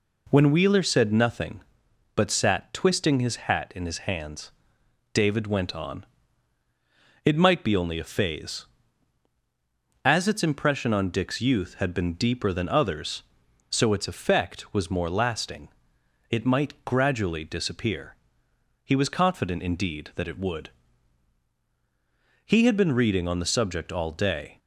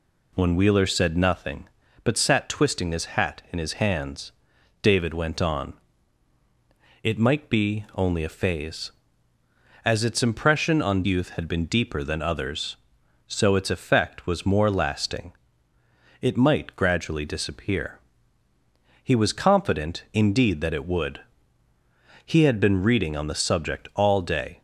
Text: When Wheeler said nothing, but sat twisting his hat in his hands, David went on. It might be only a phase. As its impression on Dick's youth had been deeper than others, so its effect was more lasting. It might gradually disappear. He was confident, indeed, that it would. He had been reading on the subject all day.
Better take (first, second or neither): first